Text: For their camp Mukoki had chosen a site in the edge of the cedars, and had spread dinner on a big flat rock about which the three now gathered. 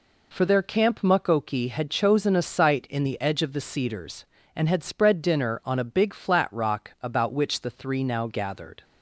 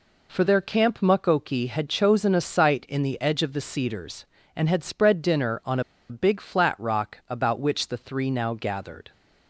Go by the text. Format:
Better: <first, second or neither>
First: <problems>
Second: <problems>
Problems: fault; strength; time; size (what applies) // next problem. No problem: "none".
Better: first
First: none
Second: pauses between "on" and "a"; slight; at 5.8 s; 0.28 s long